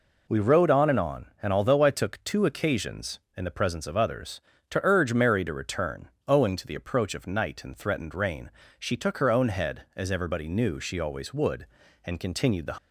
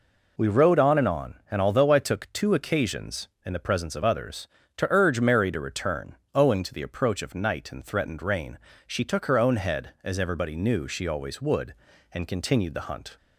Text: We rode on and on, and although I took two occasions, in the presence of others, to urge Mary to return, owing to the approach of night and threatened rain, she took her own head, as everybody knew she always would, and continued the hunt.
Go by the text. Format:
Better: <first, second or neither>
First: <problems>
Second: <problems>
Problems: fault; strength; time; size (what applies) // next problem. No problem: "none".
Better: second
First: stops before "hunt"; at 12.7 s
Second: none